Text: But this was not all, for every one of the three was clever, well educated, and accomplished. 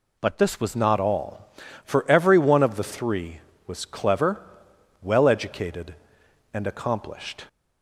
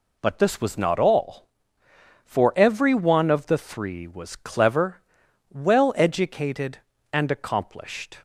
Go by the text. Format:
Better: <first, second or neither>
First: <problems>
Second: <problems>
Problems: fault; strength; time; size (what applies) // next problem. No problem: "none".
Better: second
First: changes voice at "not"; from 0.7 s on; 6.7 s long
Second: none